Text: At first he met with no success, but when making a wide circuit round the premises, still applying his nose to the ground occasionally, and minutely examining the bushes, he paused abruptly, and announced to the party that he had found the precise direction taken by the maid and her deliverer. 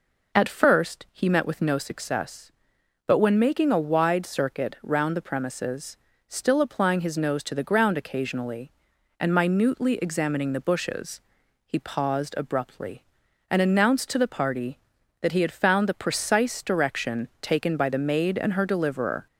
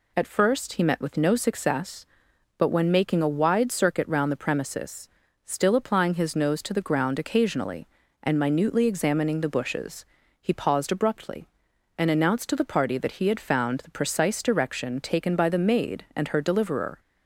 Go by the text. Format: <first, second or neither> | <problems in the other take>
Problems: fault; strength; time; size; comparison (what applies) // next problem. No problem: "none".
neither | none